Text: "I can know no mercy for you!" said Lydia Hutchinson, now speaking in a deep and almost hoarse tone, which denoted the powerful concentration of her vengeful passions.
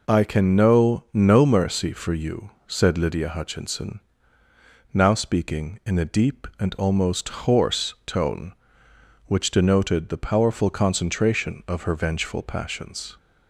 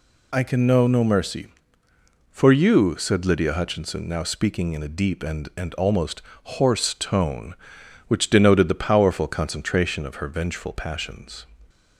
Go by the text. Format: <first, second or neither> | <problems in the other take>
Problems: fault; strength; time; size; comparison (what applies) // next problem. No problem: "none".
first | says "and" twice; at 5.5 s // pauses between "almost" and "hoarse"; slight; at 6.2 s; 0.22 s long; slight in the first